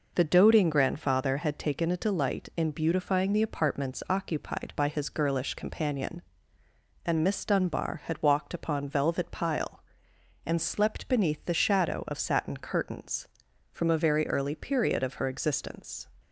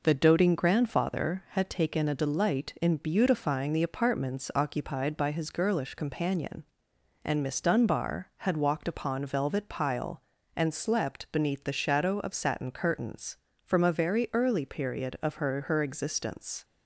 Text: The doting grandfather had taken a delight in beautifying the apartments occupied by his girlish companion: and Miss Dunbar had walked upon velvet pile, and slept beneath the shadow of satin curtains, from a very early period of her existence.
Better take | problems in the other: first | says "her" twice; at 15.6 s

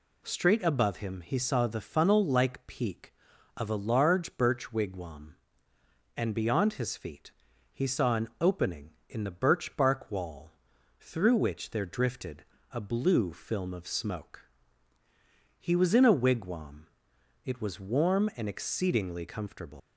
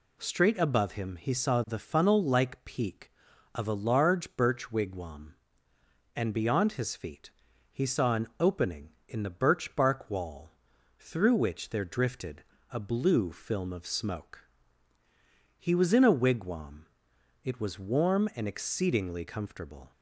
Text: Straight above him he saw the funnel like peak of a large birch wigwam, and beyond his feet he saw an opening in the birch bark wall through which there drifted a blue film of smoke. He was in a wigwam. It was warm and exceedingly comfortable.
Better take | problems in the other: second | pauses between "feet" and "he"; at 7.3 s; 0.40 s long; also in the second // pauses between "wall" and "through"; noticeable; at 10.5 s; 0.48 s long; noticeable in the second // pauses between "drifted" and "a"; slight; at 12.4 s; 0.26 s long; slight in the second // leaves "comfortable" unfinished; at 19.7 s; 125 ms

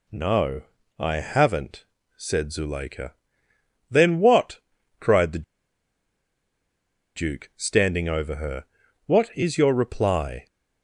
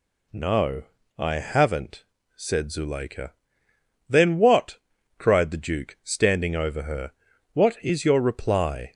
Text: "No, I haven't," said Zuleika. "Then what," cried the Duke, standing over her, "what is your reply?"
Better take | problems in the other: second | pauses between "the" and "Duke"; strong; at 5.4 s; 1.7 s long

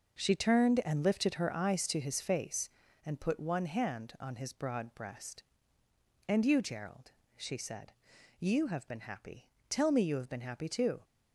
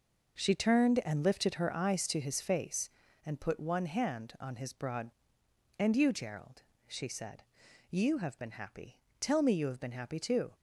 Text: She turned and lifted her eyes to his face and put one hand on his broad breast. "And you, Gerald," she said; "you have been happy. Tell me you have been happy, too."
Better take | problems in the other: first | skips "breast"; at 5.4 s

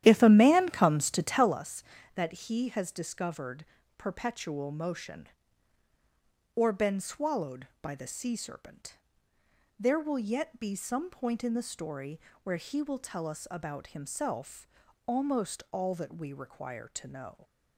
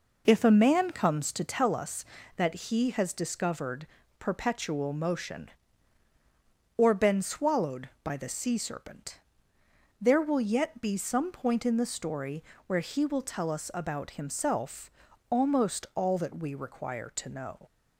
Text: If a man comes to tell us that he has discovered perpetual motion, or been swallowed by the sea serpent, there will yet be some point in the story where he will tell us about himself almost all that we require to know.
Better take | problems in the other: second | starts louder than the rest; strong; until 1.6 s; 11.5 dB // pauses between "discovered" and "perpetual"; slight; at 3.6 s; 0.32 s long; slight in the second // pauses between "story" and "where"; slight; at 12.1 s; 0.24 s long; slight in the second // pauses between "himself" and "almost"; at 14.6 s; 0.40 s long; also in the second

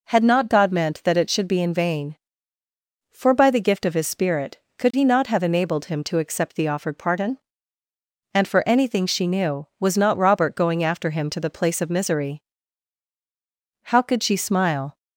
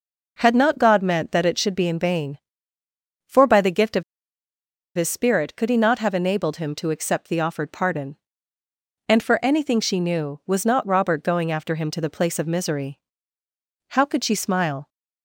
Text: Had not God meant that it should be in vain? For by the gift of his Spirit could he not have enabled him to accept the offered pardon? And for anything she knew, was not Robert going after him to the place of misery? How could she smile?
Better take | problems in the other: first | pauses between "of" and "his"; noticeable; at 4.0 s; 0.93 s long

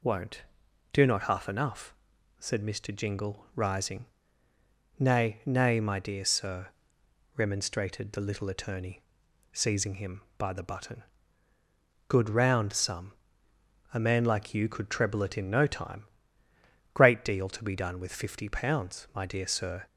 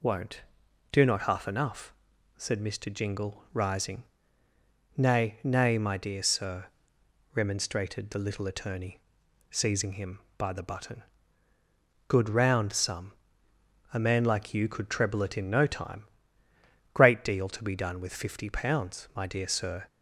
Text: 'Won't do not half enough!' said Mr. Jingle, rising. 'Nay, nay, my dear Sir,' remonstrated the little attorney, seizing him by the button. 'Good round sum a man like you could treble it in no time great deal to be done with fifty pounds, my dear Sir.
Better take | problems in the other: neither | pauses between "sum" and "a"; noticeable; the same in both // pauses between "time" and "great"; noticeable; the same in both

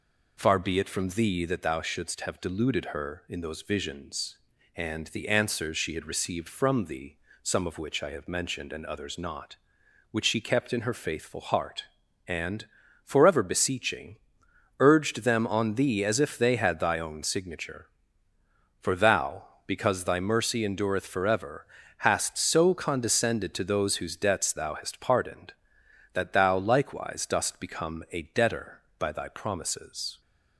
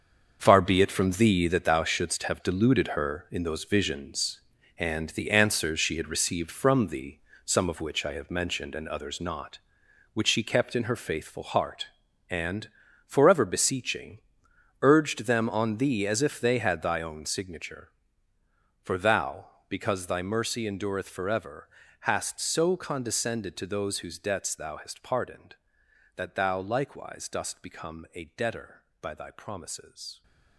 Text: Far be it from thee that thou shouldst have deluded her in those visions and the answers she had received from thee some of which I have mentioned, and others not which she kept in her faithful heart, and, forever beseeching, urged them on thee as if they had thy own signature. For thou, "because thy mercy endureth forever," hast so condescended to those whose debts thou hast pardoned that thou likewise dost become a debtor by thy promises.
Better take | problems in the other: first | gets quieter; strong; throughout; 11 dB // pauses between "thee" and "some"; slight; at 7.1 s; 0.26 s long; slight in the first

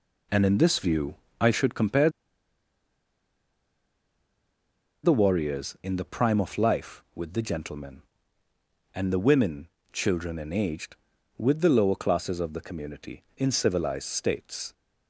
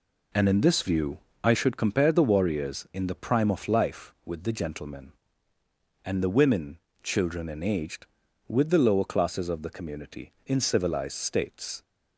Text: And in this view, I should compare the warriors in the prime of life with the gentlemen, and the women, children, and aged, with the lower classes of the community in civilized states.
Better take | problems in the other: second | pauses between "compare" and "the"; strong; at 2.0 s; 2.9 s long

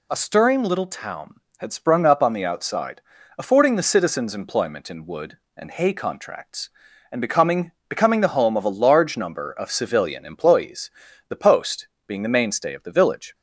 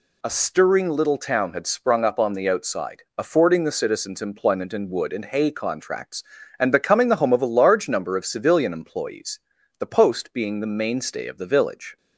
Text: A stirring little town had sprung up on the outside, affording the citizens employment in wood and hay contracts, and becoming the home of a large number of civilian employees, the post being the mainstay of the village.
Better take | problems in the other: second | says "becoming" twice; at 7.9 s // pauses between "post" and "being"; slight; at 11.8 s; 0.18 s long

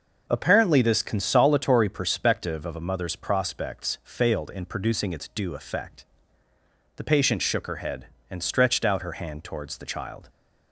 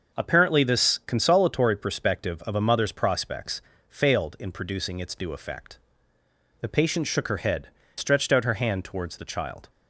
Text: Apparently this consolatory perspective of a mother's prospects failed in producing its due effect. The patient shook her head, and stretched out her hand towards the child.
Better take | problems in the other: first | starts louder than the rest; until 1.2 s; 6 dB // pauses between "prospects" and "failed"; slight; at 3.6 s; 0.26 s long // skips "and"; at 7.8 s

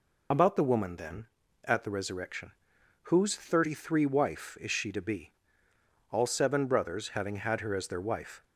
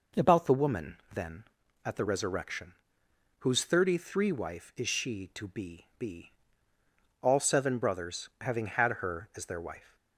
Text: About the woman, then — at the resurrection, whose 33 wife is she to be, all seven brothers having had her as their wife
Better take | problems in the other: first | says "be" twice; at 5.9 s

